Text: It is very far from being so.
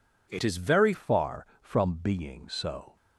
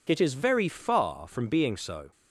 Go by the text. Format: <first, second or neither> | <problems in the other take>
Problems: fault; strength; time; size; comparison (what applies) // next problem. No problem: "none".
second | changes voice at "far"; from 0.9 s on; 2.0 s long